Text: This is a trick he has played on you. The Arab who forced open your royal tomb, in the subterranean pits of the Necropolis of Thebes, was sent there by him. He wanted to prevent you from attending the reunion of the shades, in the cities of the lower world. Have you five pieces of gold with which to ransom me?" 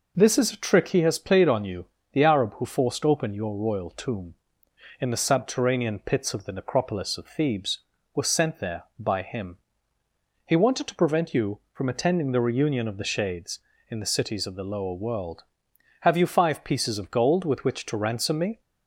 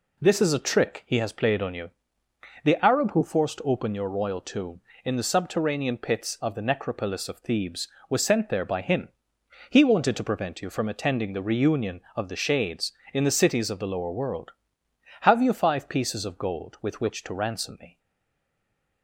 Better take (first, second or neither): first